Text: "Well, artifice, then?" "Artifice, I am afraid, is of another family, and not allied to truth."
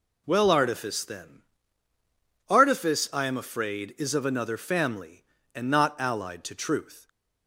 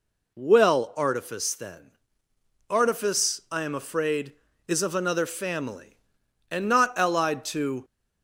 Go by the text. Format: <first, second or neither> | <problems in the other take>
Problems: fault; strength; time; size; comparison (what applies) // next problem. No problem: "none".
first | stops before "truth"; at 7.8 s